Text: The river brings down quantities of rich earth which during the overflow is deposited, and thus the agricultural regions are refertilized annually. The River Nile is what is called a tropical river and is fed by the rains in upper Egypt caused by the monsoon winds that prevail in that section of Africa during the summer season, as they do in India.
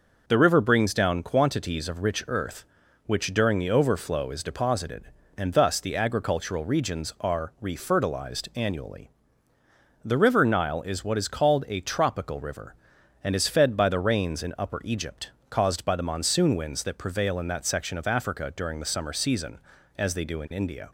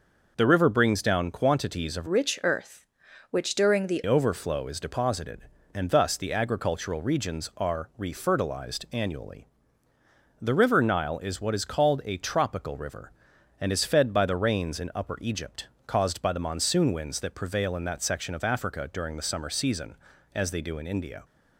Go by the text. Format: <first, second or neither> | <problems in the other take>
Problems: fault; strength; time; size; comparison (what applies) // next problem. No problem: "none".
first | changes voice from "rich" to "the"; from 2.0 to 3.9 s; 1.9 s long // pauses between "Egypt" and "caused"; slight; at 15.6 s; 0.20 s long; slight in the first